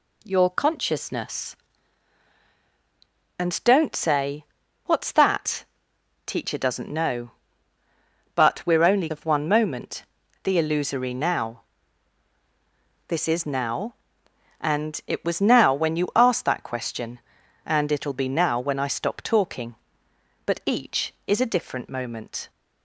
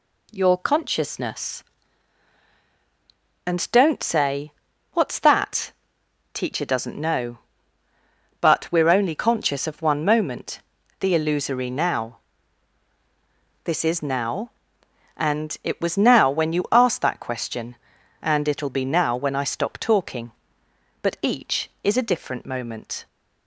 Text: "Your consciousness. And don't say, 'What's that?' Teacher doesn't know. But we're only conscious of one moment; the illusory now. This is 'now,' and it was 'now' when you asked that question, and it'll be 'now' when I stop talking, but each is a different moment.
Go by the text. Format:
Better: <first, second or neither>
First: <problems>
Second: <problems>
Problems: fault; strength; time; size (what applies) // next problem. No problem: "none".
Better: second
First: skips "conscious"; at 9.0 s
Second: none